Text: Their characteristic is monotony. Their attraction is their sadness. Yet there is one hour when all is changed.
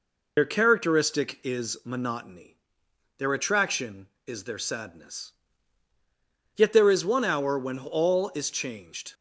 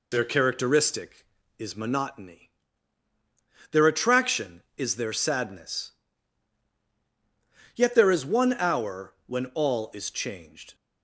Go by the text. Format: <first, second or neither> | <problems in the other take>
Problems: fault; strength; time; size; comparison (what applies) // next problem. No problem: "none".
second | loses the start of "Their"; at 0.3 s; 60 ms